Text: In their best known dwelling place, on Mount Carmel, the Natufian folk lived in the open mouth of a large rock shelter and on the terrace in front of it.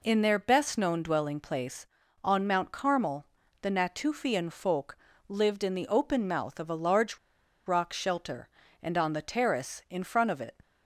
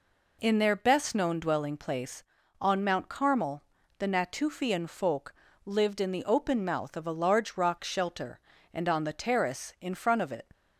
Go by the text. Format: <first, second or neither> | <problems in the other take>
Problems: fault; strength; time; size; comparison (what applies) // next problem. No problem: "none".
second | pauses between "folk" and "lived"; slight; at 4.9 s; 0.32 s long; slight in the second // pauses between "large" and "rock"; noticeable; at 7.1 s; 0.49 s long